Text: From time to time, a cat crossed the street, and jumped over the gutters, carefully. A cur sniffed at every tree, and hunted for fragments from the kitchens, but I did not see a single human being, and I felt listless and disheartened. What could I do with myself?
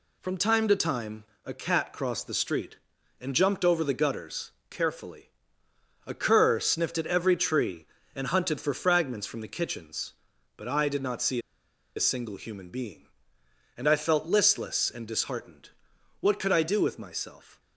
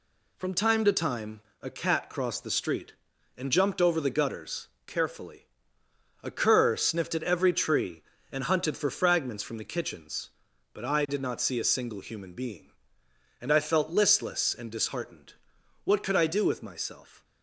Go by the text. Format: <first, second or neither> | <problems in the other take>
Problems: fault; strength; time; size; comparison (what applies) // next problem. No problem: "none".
second | pauses between "see" and "a"; noticeable; at 11.3 s; 0.57 s long